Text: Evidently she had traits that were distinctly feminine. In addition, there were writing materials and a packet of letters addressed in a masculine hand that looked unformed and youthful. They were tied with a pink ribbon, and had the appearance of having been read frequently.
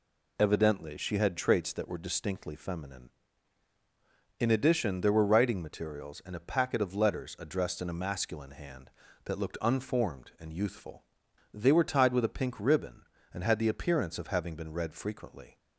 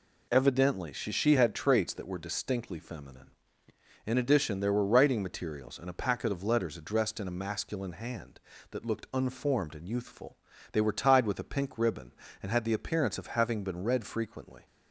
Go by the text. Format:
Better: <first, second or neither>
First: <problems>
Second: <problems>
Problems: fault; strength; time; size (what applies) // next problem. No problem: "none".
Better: first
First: none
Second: says "she" twice; at 1.1 s